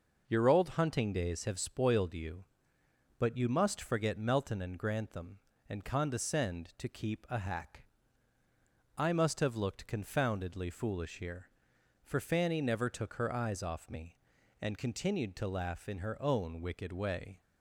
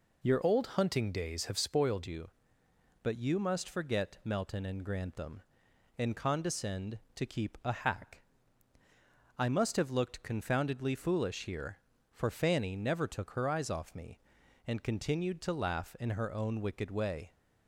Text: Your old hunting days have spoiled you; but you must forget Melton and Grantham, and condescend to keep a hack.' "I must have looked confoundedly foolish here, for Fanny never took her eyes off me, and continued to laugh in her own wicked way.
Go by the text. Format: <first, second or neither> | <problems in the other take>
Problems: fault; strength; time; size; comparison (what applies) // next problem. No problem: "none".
first | changes voice from "old" to "spoiled"; from 0.4 to 2.0 s; 1.6 s long